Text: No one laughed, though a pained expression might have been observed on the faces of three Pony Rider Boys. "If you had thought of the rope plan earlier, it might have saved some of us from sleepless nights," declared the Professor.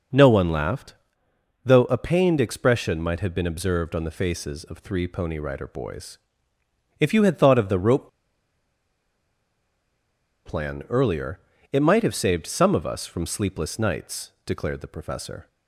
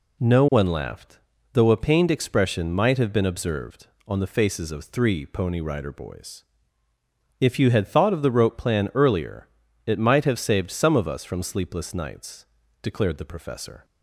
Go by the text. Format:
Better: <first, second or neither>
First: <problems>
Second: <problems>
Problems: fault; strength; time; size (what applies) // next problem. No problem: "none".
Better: second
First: pauses between "rope" and "plan"; strong; at 8.0 s; 2.3 s long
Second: none